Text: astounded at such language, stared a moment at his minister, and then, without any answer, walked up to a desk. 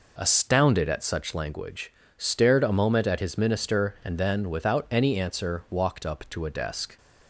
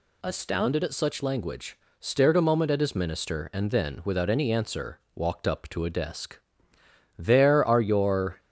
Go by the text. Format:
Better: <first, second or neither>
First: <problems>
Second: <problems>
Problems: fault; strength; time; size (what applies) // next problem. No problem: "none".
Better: first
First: none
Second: goes on to say "There are your"; noticeable; from 7.1 s on; 1.2 s long